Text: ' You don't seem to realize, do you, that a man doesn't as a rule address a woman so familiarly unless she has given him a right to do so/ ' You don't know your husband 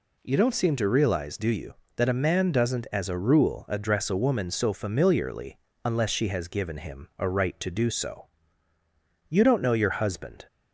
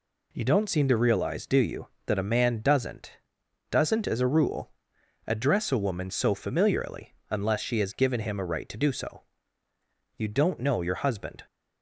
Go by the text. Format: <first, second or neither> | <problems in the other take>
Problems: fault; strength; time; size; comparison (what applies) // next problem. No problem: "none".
first | says "doesn't" twice; at 3.6 s // pauses between "rule" and "address"; noticeable; at 4.7 s; 0.56 s long // pauses between "familiarly" and "unless"; slight; at 7.1 s; 0.16 s long; slight in the first